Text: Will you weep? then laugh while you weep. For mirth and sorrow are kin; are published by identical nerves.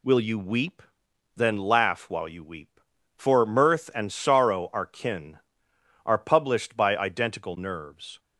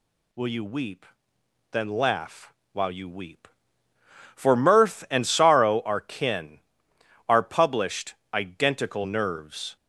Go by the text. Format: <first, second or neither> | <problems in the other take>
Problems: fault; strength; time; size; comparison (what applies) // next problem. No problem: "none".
first | pauses between "laugh" and "while"; slight; at 2.5 s; 0.22 s long // skips "by"; at 8.2 s